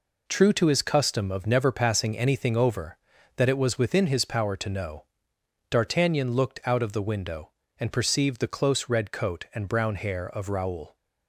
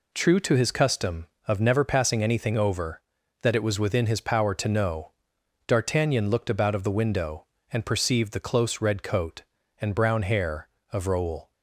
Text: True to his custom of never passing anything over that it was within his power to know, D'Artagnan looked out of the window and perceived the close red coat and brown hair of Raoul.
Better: first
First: none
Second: says "about" for "out"; at 6.4 s

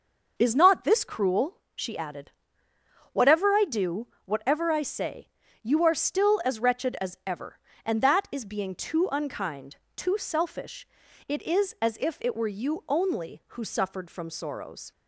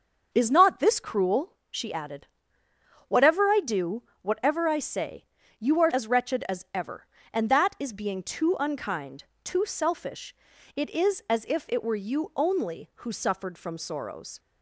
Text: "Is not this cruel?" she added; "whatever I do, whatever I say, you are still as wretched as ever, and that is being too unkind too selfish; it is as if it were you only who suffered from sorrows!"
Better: first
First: pauses between "unkind" and "too"; slight; at 9.7 s; 0.18 s long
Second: starts louder than the rest; noticeable; until 1.3 s; 6 dB // skips "still"; at 5.9 s // pauses between "unkind" and "too"; slight; at 9.2 s; 0.18 s long

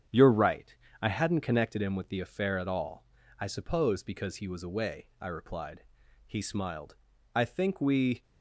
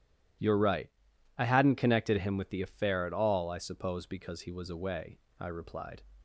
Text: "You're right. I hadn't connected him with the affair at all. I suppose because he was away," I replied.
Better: second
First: starts louder than the rest; strong; until 1.3 s; 8 dB // goes on to say "He smiled I think we"; strong; from 6.2 s on; 1.9 s long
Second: none

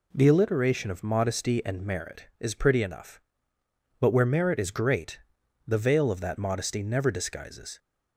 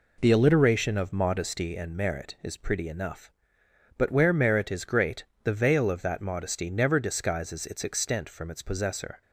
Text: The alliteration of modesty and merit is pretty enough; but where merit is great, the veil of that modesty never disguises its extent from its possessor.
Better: second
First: stops before "its extent from its possessor"; at 7.7 s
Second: none

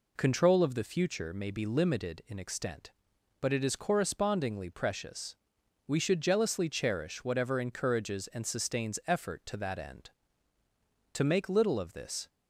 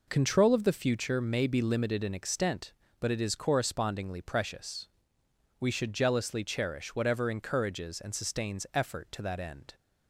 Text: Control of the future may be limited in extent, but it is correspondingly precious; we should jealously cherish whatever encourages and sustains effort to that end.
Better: second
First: goes on to say "To make little of this"; noticeable; from 11.1 s on; 1.1 s long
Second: none

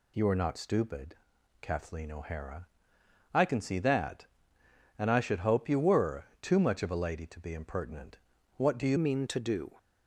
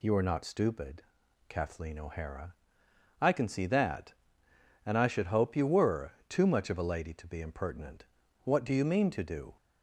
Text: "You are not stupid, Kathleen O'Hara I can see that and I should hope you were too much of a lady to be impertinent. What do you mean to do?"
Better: second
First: pauses between "O'Hara" and "I"; noticeable; at 2.6 s; 0.64 s long // pauses between "were" and "too"; slight; at 6.2 s; 0.18 s long // changes voice at "mean"; from 8.9 s on; 0.8 s long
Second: pauses between "O'Hara" and "I"; noticeable; at 2.5 s; 0.64 s long // pauses between "were" and "too"; slight; at 6.0 s; 0.18 s long

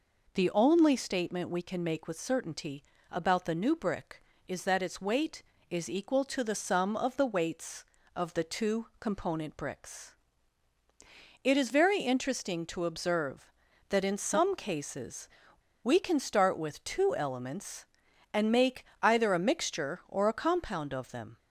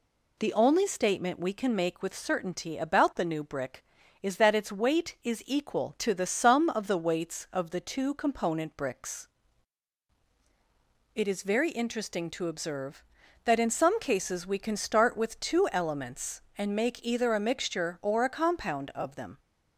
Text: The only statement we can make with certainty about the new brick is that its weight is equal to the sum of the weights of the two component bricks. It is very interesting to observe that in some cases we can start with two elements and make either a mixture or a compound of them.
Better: second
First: pauses between "certainty" and "about"; slight; at 2.8 s; 0.26 s long // pauses between "cases" and "we"; noticeable; at 15.2 s; 0.55 s long // pauses between "make" and "either"; slight; at 18.8 s; 0.16 s long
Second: none

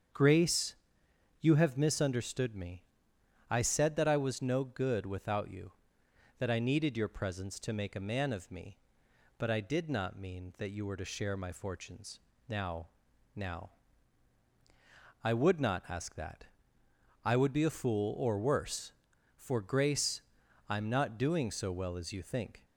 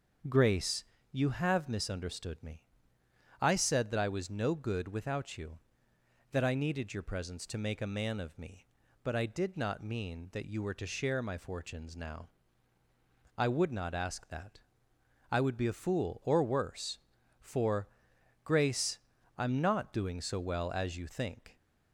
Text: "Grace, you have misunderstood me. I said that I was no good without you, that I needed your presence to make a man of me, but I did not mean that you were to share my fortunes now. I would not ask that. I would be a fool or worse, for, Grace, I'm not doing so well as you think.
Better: second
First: starts louder than the rest; strong; until 1.7 s; 7.5 dB // pauses between "fortunes" and "now"; slight; at 12.1 s; 0.26 s long // says "now" twice; at 13.3 s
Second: starts louder than the rest; until 1.5 s; 6.5 dB

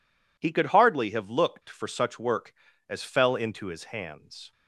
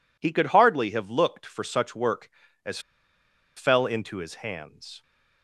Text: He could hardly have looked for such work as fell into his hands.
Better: first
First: none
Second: pauses between "as" and "fell"; noticeable; at 2.7 s; 0.76 s long

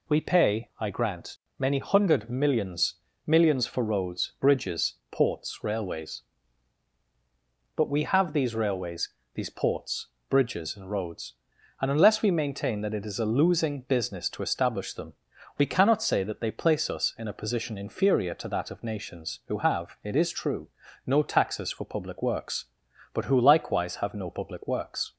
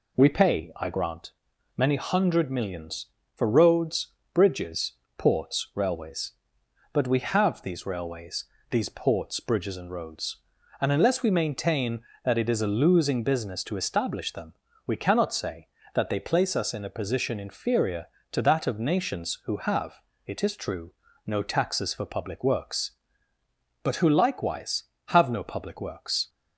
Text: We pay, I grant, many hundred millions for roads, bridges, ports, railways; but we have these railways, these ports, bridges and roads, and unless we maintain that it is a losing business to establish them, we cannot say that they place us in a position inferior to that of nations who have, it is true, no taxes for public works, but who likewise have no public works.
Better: second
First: says "millions" twice; at 3.2 s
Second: none

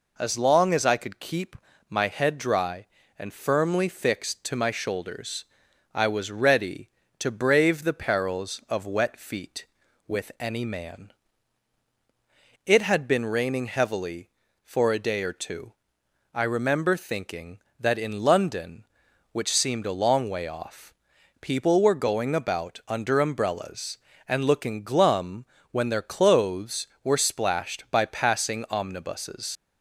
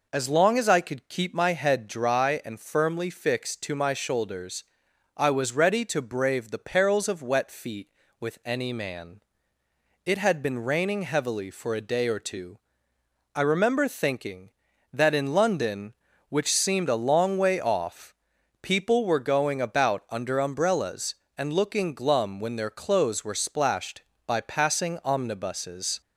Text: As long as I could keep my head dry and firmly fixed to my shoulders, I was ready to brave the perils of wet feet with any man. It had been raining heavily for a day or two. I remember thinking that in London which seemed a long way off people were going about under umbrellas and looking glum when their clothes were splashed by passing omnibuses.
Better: second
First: pauses between "keep" and "my"; slight; at 1.5 s; 0.34 s long // pauses between "off" and "people"; noticeable; at 20.9 s; 0.48 s long // pauses between "glum" and "when"; slight; at 25.4 s; 0.28 s long // leaves "omnibuses" unfinished; at 29.5 s; 105 ms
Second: pauses between "off" and "people"; noticeable; at 18.1 s; 0.48 s long

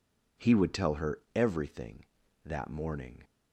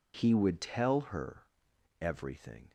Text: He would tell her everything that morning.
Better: first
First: none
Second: pauses between "her" and "everything"; noticeable; at 1.4 s; 0.56 s long // stops before "that morning"; at 2.6 s

